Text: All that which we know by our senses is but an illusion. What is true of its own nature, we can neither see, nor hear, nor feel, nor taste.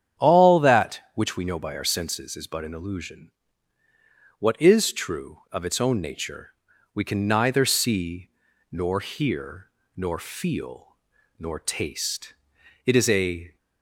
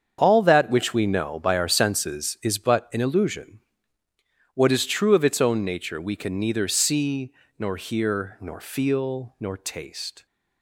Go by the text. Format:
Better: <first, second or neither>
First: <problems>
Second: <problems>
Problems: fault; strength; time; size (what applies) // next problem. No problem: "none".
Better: second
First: starts louder than the rest; strong; until 1.3 s; 9 dB // goes on to say "It is a"; noticeable; from 12.8 s on; 0.72 s long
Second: starts louder than the rest; strong; until 1.2 s; 7.5 dB